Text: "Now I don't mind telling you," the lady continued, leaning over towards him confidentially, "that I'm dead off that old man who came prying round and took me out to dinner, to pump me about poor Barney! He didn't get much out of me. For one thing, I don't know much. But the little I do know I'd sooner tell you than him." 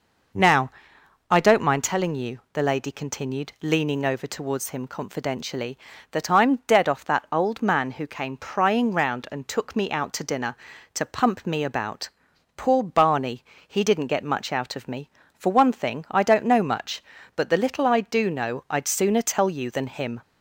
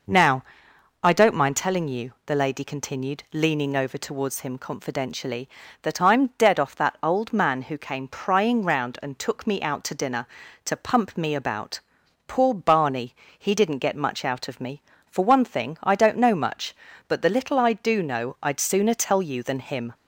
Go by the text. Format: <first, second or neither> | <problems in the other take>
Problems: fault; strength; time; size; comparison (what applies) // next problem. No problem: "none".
neither | pauses between "Now" and "I"; noticeable; the same in both // pauses between "about" and "poor"; noticeable; the same in both